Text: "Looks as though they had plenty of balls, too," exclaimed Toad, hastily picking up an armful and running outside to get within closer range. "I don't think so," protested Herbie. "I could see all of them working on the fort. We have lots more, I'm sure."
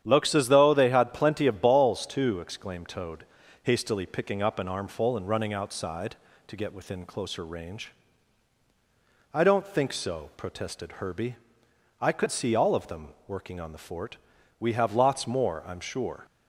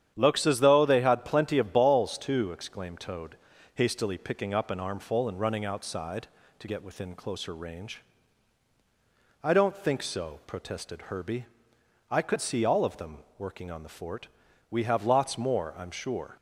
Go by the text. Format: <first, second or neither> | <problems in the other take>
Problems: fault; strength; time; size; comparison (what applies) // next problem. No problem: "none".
neither | starts louder than the rest; strong; the same in both